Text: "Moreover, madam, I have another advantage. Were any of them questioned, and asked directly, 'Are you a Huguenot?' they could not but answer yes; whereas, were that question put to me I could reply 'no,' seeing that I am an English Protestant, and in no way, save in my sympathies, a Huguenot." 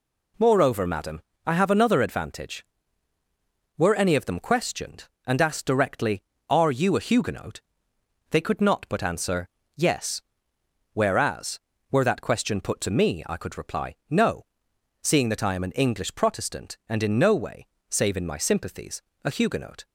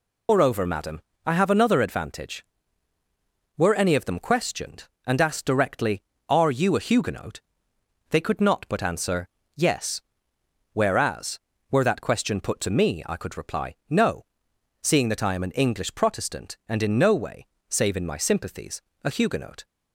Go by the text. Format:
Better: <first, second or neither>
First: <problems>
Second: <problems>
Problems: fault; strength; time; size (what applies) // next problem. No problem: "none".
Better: first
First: pauses between "answer" and "yes"; slight; at 9.4 s; 0.30 s long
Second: loses the start of "Moreover"; at 0.2 s; 135 ms // pauses between "answer" and "yes"; slight; at 9.2 s; 0.30 s long